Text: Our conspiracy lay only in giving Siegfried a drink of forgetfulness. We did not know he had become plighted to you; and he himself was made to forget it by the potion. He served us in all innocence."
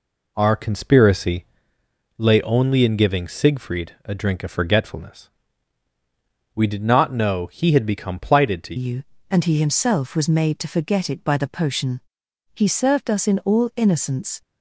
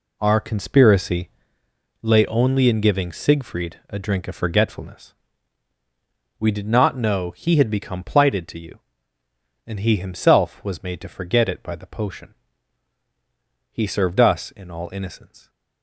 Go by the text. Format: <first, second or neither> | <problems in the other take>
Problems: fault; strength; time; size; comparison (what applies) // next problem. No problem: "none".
second | pauses between "conspiracy" and "lay"; noticeable; at 1.4 s; 0.74 s long; noticeable in the second // changes voice at "you"; from 8.7 s on; 5.7 s long